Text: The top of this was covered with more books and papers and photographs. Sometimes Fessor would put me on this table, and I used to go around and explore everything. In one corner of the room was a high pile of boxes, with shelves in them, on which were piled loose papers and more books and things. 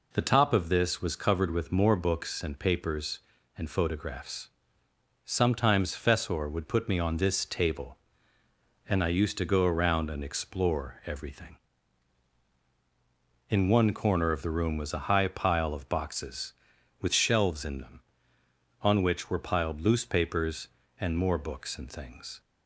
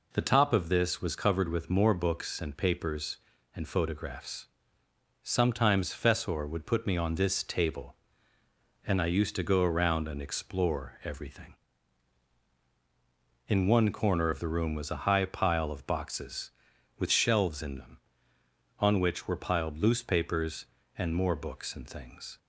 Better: neither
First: none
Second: none

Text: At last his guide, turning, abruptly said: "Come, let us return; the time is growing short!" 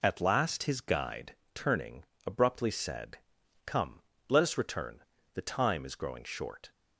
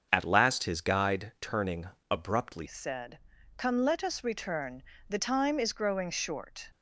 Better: first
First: none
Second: starts louder than the rest; until 1.1 s; 7 dB // changes voice at "said"; from 2.6 s on; 4.1 s long

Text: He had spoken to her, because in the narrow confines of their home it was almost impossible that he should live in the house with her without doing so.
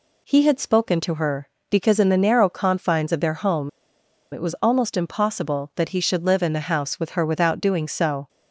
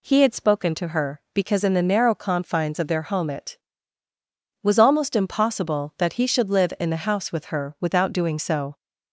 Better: second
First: pauses between "home" and "it"; noticeable; at 3.6 s; 0.62 s long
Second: none

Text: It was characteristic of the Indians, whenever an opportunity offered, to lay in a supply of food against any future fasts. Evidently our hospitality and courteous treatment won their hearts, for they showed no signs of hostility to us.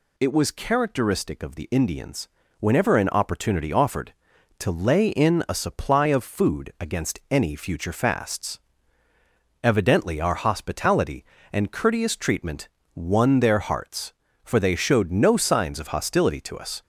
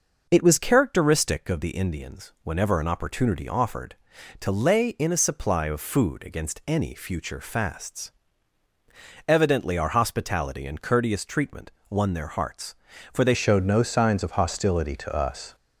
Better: first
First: pauses between "treatment" and "won"; slight; at 12.6 s; 0.24 s long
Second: pauses between "treatment" and "won"; slight; at 11.7 s; 0.18 s long // changes voice at "showed"; from 13.3 s on; 2.2 s long

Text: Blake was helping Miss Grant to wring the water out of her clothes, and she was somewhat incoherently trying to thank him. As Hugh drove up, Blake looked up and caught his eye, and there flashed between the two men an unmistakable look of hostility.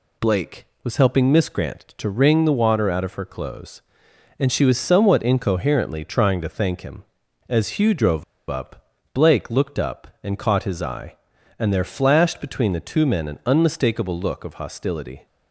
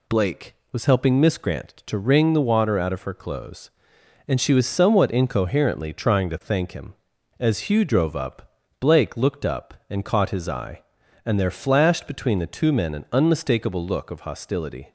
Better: second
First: pauses between "drove" and "up"; slight; at 8.2 s; 0.25 s long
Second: none

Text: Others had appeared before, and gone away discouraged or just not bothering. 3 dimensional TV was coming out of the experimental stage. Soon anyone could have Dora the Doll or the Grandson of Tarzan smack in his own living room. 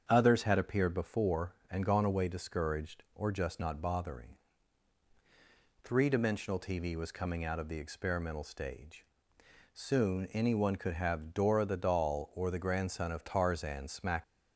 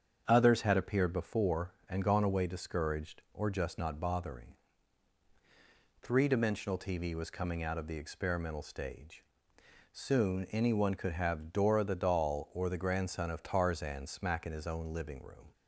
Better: second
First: starts louder than the rest; strong; until 1.1 s; 7.5 dB // stops before "in his own living room"; at 14.2 s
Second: starts louder than the rest; strong; until 1.2 s; 7.5 dB

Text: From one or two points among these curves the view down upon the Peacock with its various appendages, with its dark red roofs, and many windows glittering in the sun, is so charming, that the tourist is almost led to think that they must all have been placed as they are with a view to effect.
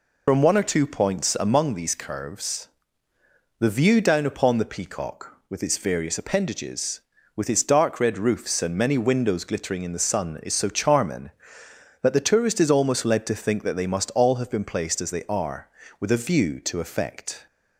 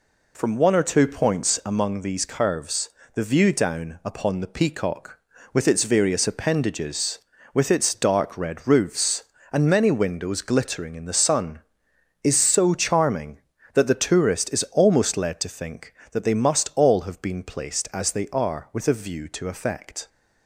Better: second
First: loses the start of "From"; at 0.2 s; 95 ms // pauses between "curves" and "the"; noticeable; at 2.6 s; 0.94 s long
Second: pauses between "curves" and "the"; slight; at 2.8 s; 0.24 s long

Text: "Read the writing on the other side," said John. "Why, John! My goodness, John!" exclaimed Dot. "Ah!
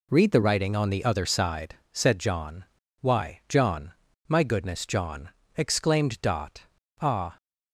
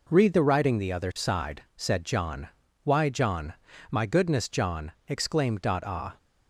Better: first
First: none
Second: skips "on"; at 0.7 s

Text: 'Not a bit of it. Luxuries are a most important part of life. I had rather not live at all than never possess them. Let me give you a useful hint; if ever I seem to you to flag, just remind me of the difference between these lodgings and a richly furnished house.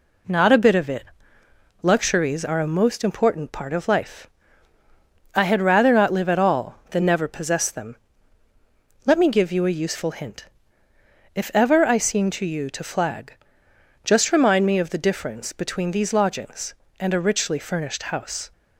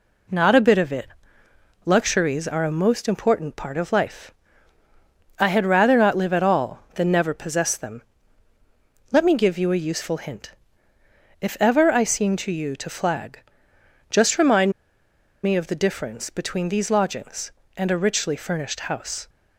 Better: first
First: none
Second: pauses between "remind" and "me"; noticeable; at 14.6 s; 0.74 s long

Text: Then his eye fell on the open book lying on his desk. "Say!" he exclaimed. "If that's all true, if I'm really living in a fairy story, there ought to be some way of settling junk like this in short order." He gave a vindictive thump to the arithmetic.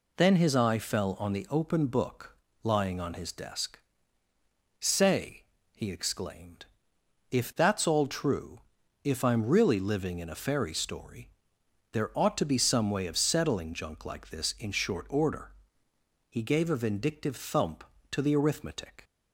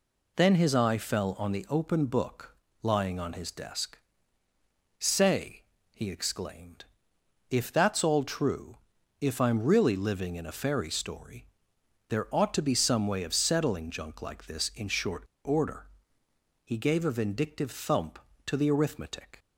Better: first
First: pauses between "book" and "lying"; slight; at 2.3 s; 0.28 s long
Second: pauses between "book" and "lying"; slight; at 2.5 s; 0.28 s long // pauses between "short" and "order"; slight; at 15.2 s; 0.22 s long

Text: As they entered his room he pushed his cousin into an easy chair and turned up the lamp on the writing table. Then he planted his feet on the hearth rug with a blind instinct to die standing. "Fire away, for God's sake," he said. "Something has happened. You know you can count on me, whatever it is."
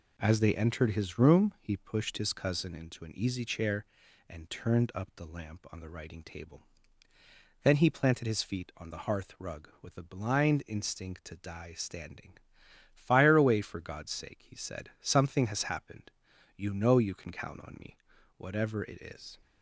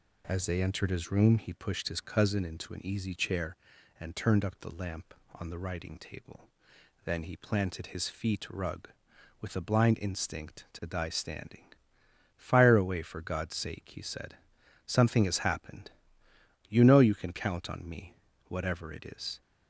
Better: first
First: none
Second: skips "on the hearth"; at 8.4 s

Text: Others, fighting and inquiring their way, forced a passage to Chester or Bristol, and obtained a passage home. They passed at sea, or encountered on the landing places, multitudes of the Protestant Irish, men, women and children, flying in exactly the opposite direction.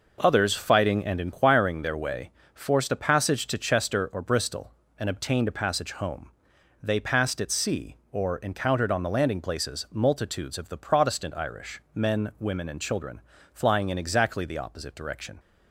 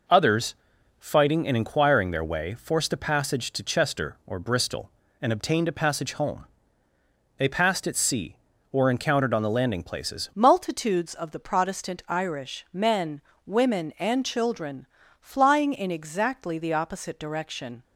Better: first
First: none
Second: changes voice at "multitudes"; from 10.3 s on; 7.5 s long

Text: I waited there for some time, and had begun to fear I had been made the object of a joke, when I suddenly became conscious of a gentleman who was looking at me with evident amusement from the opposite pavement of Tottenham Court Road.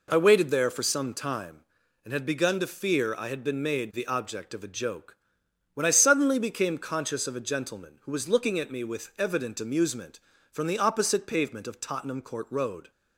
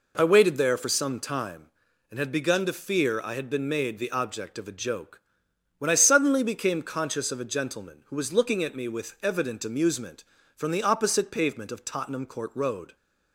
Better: neither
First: none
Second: none

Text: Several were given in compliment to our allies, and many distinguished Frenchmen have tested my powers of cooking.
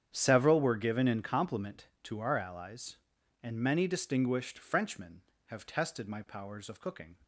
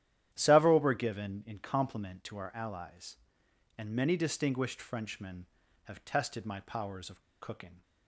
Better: first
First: starts louder than the rest; strong; until 1.1 s; 8.5 dB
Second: starts louder than the rest; strong; until 1.3 s; 11.5 dB // pauses between "of" and "cooking"; slight; at 7.2 s; 0.19 s long

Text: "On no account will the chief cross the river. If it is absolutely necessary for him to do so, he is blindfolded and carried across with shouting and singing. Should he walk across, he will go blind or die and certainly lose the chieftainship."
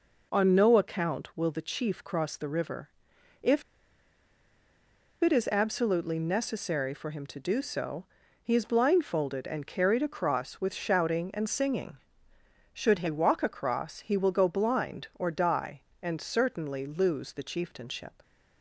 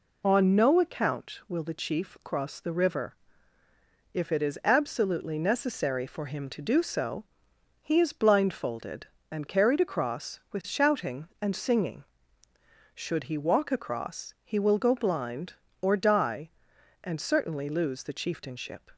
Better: second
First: pauses between "If" and "it"; strong; at 3.6 s; 1.5 s long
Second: none

